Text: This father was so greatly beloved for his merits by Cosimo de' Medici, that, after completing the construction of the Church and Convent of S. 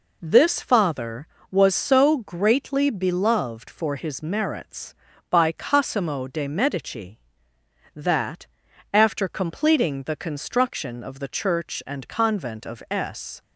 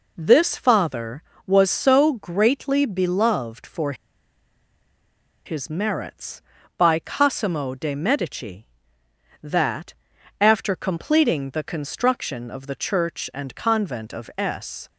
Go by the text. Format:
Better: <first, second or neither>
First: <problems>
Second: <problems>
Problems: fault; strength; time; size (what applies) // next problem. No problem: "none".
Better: first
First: none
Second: pauses between "for" and "his"; strong; at 3.9 s; 1.5 s long